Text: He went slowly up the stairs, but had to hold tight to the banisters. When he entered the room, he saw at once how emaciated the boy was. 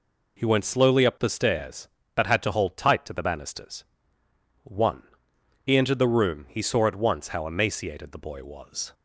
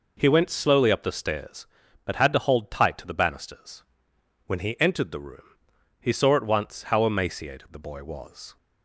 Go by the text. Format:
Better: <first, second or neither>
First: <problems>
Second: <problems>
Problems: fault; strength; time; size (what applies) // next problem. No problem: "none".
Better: second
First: says "One" for "When"; at 4.6 s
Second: none